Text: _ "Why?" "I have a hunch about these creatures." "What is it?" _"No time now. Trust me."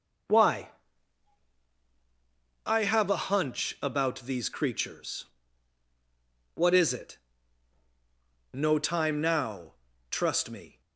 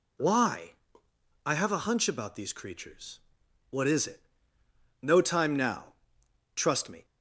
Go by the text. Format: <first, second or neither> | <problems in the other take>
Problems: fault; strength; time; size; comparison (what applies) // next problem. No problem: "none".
neither | none